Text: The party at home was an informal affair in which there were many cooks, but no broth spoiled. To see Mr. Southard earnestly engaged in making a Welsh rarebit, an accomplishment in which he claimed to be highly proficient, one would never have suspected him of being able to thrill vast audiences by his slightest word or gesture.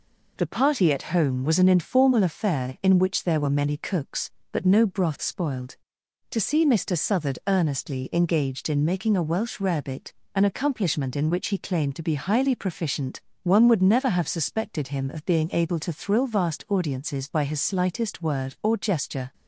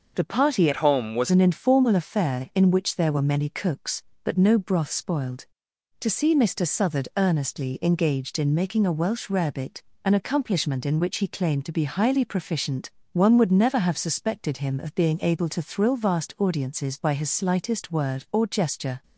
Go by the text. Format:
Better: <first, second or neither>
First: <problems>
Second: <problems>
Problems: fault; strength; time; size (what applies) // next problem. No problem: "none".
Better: first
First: none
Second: changes voice from "at" to "was"; from 0.7 to 1.3 s; 0.6 s long